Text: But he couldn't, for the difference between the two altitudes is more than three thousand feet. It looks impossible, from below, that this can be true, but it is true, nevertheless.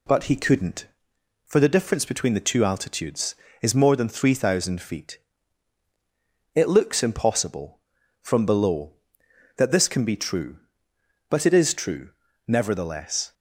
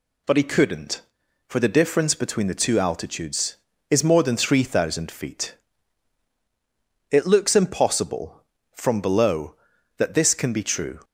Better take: first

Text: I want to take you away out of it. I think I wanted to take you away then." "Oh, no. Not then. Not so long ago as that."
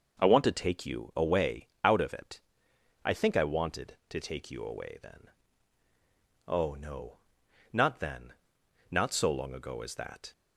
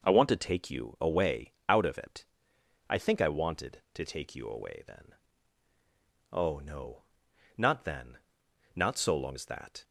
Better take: first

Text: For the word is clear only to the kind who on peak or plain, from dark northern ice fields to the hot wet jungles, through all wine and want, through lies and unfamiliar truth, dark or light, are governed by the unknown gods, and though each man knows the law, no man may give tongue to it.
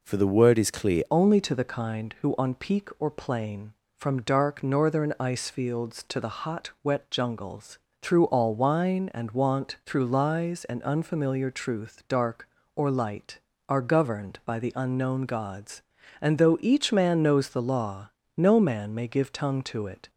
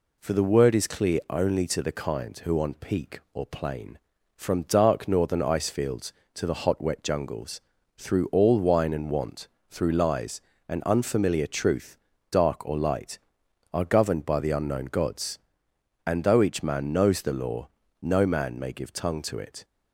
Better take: second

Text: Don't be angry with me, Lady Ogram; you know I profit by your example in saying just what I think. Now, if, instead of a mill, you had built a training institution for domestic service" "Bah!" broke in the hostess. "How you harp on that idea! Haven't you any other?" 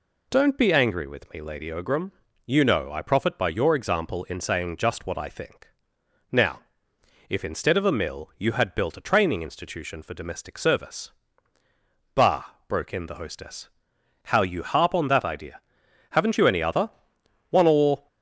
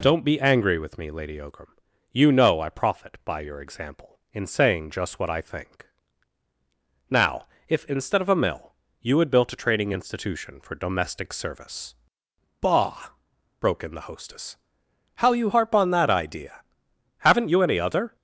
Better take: second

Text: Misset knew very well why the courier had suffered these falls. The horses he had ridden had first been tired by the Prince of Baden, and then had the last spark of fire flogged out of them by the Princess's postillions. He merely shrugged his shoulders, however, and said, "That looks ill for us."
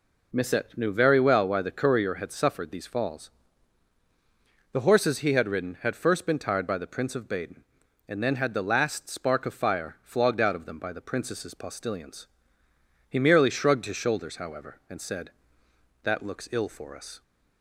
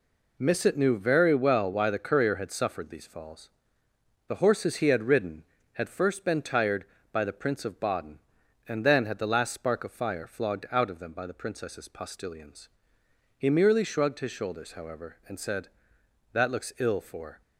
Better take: first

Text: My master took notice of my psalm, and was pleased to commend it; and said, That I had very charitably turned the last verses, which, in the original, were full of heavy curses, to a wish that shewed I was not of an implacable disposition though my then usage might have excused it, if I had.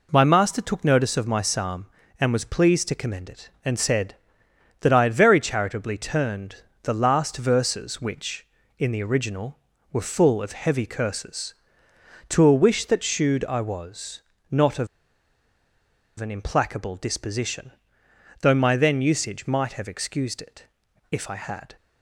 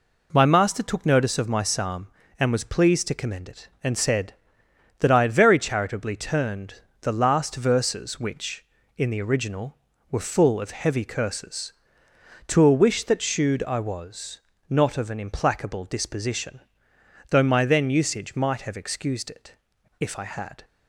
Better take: second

